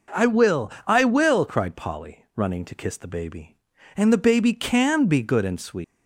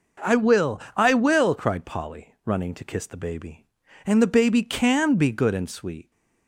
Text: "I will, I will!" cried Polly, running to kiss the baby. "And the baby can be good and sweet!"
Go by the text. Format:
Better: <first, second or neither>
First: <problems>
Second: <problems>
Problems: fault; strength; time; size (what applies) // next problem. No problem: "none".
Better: second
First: leaves "sweet" unfinished; at 5.8 s; 165 ms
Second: none